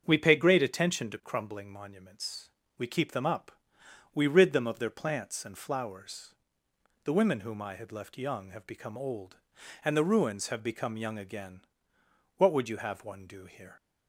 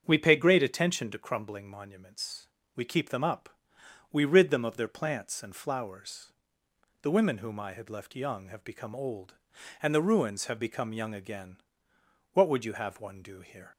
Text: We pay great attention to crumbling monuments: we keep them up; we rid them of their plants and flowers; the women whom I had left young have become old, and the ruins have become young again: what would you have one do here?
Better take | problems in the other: neither | starts louder than the rest; strong; the same in both

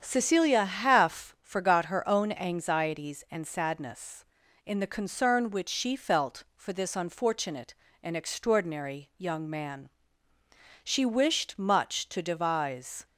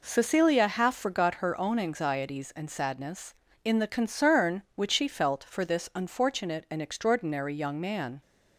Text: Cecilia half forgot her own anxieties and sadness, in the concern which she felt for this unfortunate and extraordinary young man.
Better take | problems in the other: second | starts louder than the rest; strong; until 1.0 s; 8 dB // goes on to say "She wished much to devise"; strong; from 10.8 s on; 2.2 s long

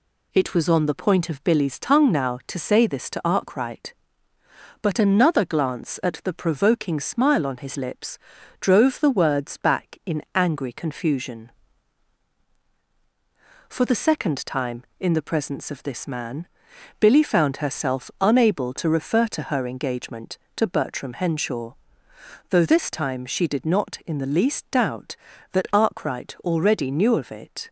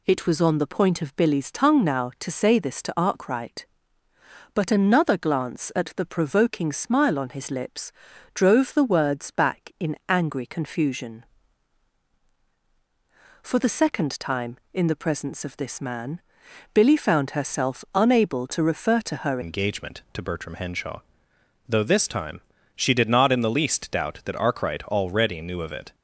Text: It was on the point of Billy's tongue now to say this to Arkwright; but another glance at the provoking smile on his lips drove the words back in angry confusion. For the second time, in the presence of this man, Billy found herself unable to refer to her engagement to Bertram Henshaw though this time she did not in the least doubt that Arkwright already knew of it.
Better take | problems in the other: first | pauses between "lips" and "drove"; at 7.8 s; 0.44 s long; also in the first // changes voice at "engagement"; from 19.4 s on; 6.5 s long // pauses between "Henshaw" and "though"; noticeable; at 21.0 s; 0.66 s long; noticeable in the first // pauses between "time" and "she"; slight; at 22.4 s; 0.34 s long

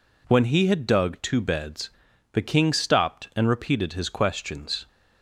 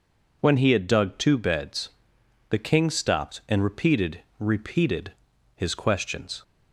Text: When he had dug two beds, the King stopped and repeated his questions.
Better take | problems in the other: first | says "repeated" twice; at 4.3 s

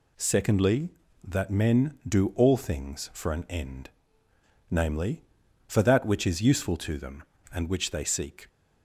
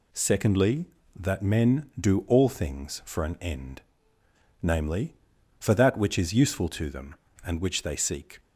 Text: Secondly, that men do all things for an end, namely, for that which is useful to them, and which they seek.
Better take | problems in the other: neither | none

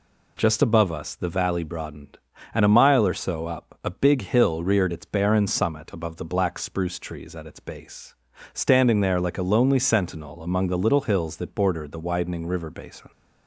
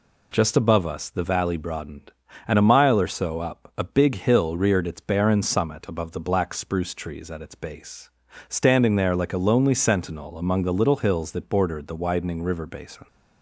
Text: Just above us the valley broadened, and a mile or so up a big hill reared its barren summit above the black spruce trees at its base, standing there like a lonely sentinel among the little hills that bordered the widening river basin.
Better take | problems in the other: neither | none

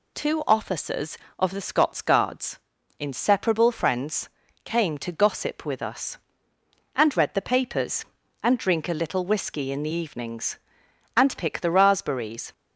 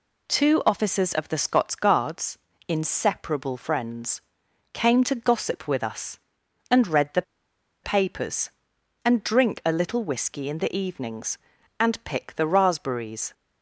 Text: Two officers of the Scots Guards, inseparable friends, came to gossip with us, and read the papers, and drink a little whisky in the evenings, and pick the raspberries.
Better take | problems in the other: first | pauses between "the" and "papers"; noticeable; at 7.2 s; 0.61 s long

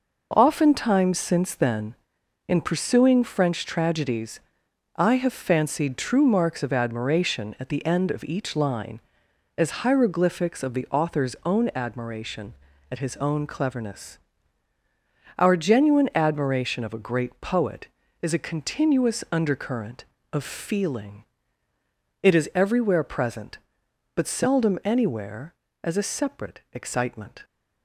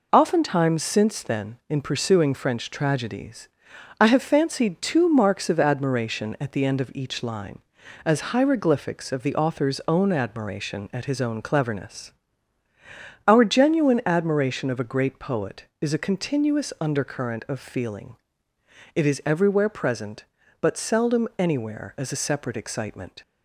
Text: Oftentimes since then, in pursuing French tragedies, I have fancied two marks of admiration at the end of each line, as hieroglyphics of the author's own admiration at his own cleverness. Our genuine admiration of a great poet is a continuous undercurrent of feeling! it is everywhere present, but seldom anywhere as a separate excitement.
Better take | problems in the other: second | says "true" for "two"; at 5.9 s

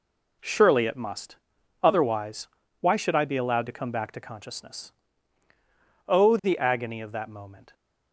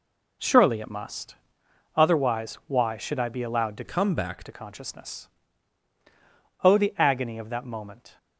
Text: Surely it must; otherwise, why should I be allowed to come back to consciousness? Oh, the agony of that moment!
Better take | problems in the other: first | changes voice from "come" to "back"; from 3.8 to 4.4 s; 0.6 s long

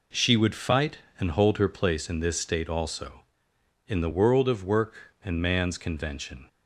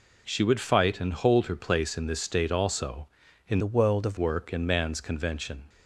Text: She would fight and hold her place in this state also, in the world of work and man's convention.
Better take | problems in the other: first | changes voice from "the" to "of"; from 3.5 to 4.1 s; 0.6 s long

